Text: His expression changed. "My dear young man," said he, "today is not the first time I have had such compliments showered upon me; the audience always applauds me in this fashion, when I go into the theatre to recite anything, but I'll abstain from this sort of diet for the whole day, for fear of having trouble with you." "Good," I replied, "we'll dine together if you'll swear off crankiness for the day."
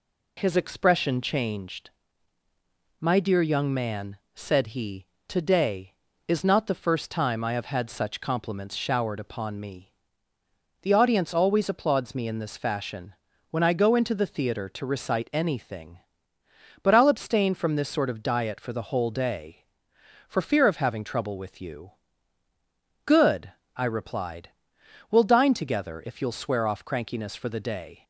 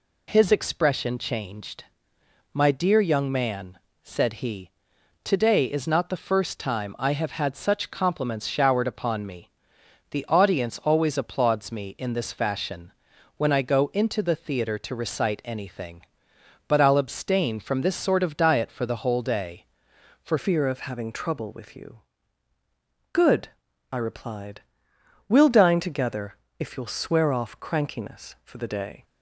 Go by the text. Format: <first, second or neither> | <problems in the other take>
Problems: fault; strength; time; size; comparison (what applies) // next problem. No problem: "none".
first | changes voice at "fear"; from 20.3 s on; 8.7 s long // pauses between "together" and "if"; slight; at 26.3 s; 0.24 s long